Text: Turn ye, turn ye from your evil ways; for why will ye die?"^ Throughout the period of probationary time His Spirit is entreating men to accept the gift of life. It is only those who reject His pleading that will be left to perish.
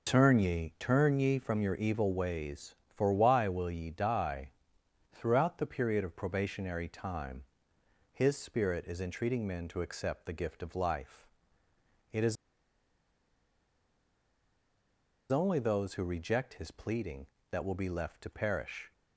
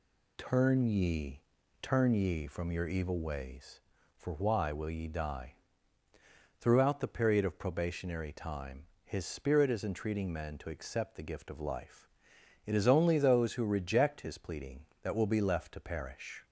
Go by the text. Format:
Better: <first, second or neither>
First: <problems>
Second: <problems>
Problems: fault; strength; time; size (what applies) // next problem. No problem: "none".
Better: second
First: pauses between "time" and "His"; noticeable; at 7.4 s; 0.70 s long // pauses between "is" and "only"; strong; at 12.3 s; 2.9 s long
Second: pauses between "time" and "His"; slight; at 8.8 s; 0.18 s long